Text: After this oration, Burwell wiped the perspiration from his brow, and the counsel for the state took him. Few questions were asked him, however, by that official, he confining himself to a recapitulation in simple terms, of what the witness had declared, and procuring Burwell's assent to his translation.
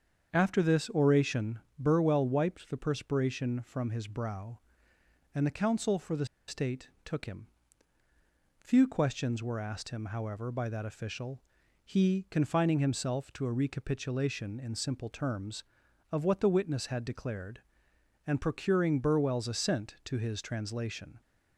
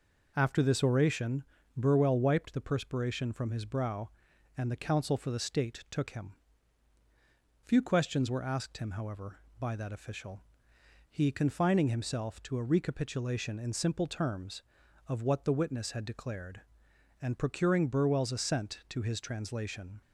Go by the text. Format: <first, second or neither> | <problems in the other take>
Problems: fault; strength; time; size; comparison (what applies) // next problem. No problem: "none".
second | starts louder than the rest; strong; until 1.3 s; 7 dB // pauses between "the" and "state"; slight; at 6.2 s; 0.23 s long // pauses between "state" and "took"; slight; at 6.8 s; 0.16 s long